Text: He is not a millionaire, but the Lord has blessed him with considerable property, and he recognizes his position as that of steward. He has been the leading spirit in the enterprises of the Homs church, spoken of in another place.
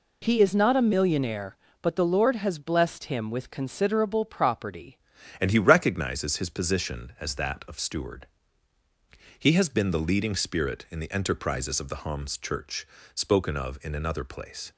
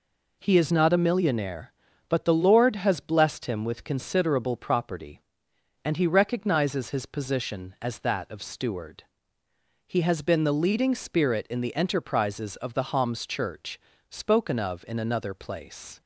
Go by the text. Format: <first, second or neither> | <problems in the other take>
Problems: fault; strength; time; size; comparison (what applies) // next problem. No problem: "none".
second | changes voice at "and"; from 5.3 s on; 9.4 s long